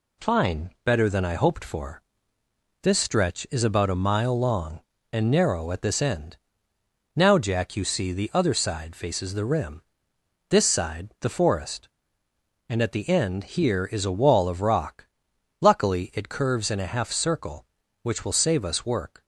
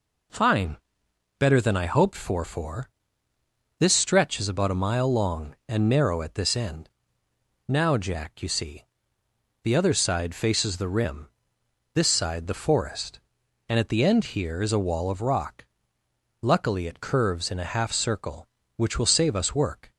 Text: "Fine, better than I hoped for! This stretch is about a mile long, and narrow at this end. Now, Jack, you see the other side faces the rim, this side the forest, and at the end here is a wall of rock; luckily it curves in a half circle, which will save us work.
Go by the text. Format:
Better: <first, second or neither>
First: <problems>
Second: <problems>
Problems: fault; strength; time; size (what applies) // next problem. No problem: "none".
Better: first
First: none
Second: says "for" twice; at 2.4 s // pauses between "see" and "the"; noticeable; at 8.8 s; 0.78 s long